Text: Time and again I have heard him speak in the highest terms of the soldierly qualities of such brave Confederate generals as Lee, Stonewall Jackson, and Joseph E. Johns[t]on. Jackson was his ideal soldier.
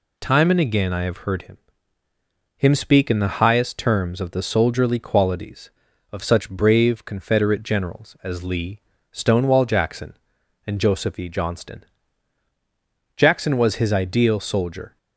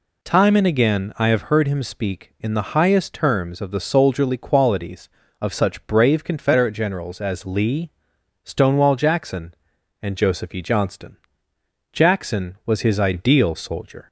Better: second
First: says "him" twice; at 2.5 s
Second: none

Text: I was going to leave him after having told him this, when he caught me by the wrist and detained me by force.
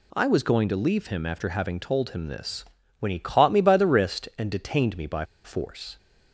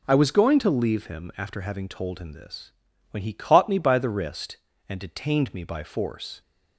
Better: second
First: pauses between "by" and "force"; slight; at 5.2 s; 0.21 s long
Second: none

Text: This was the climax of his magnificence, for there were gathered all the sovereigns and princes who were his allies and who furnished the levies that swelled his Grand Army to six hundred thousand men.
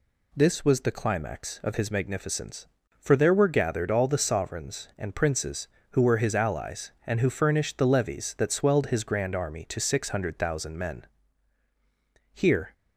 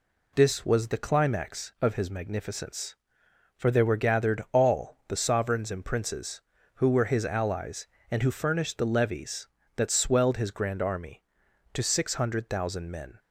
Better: second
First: goes on to say "Here"; slight; from 12.3 s on; 0.40 s long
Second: none

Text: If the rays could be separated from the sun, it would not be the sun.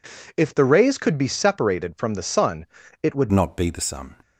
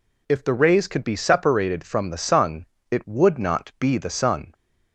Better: second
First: changes voice at "not"; from 3.3 s on; 0.8 s long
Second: none

